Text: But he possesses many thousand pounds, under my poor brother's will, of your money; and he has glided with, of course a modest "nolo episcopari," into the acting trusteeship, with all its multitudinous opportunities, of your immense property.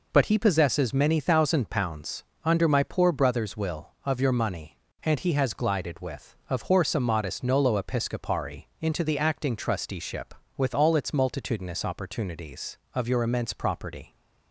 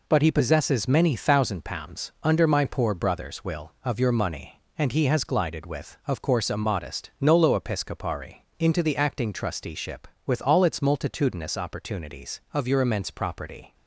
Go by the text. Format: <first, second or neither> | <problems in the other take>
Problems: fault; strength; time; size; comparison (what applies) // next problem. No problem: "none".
second | says "horse" for "course"; at 6.6 s